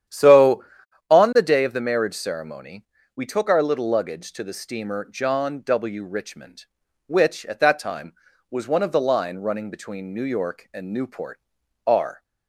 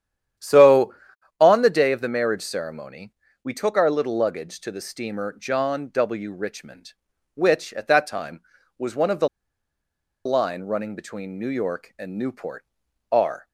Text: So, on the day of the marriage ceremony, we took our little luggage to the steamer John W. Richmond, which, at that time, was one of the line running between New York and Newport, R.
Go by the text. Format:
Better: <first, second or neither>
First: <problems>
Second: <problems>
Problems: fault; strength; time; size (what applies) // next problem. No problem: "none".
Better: first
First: starts louder than the rest; strong; until 1.5 s; 10 dB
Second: starts louder than the rest; strong; until 1.8 s; 10 dB // pauses between "the" and "line"; noticeable; at 9.2 s; 0.97 s long